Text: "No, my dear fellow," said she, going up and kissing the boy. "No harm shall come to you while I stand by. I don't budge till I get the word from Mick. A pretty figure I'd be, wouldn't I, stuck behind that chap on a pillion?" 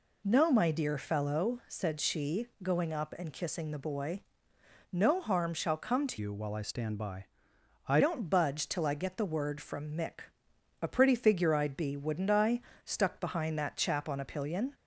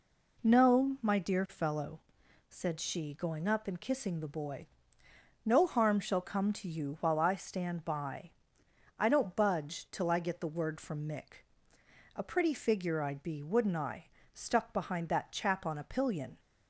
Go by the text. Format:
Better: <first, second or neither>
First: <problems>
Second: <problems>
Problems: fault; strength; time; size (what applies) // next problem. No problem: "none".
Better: second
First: changes voice from "you" to "I"; from 6.1 to 8.0 s; 1.9 s long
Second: none